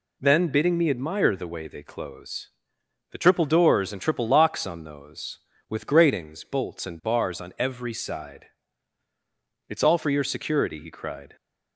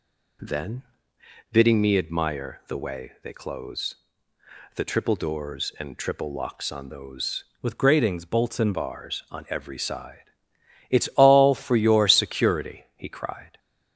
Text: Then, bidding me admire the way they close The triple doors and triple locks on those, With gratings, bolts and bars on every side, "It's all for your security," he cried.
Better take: first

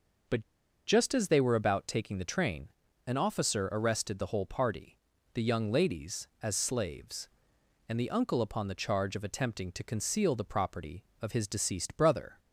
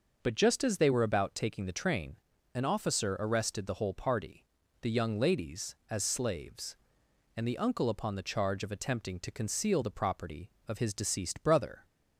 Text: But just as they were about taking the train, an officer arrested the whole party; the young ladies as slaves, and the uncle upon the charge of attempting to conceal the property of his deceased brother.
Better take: second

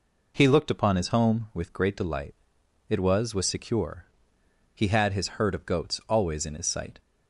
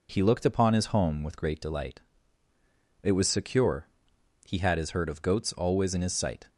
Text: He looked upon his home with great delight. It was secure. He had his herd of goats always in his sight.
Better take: second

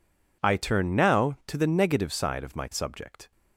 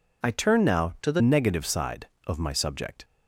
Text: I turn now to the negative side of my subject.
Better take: first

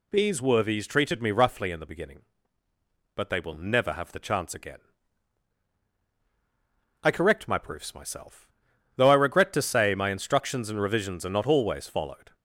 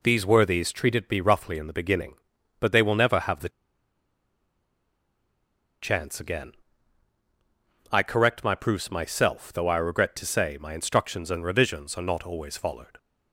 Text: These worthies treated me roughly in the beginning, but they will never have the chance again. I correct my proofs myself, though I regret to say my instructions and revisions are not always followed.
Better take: first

